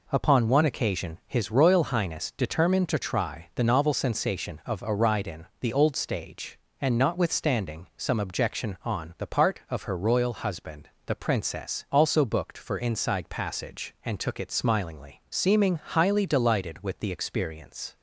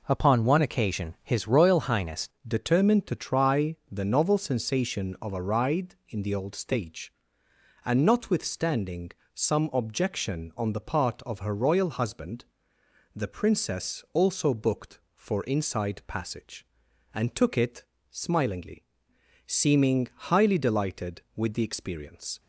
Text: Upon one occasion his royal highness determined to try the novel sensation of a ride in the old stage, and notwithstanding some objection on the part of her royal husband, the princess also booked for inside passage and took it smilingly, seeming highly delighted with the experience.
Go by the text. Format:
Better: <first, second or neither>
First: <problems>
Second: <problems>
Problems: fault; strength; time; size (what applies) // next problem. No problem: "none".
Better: first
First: none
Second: changes voice at "determined"; from 2.4 s on; 19.9 s long // pauses between "notwithstanding" and "some"; slight; at 9.0 s; 0.24 s long // pauses between "it" and "smilingly"; slight; at 17.8 s; 0.26 s long // pauses between "seeming" and "highly"; slight; at 20.0 s; 0.22 s long